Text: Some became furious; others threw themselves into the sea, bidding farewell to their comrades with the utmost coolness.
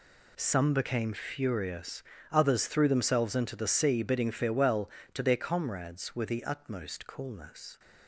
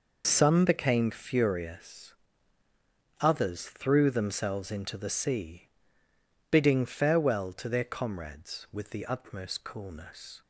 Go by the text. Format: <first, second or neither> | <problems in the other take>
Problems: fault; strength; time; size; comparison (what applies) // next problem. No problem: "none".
neither | none